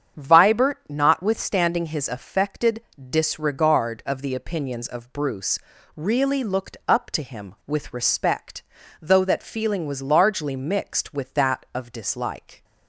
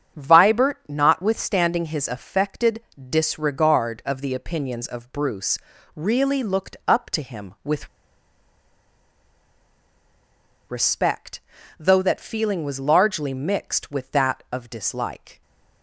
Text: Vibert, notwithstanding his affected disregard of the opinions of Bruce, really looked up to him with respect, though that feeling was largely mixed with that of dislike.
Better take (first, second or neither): first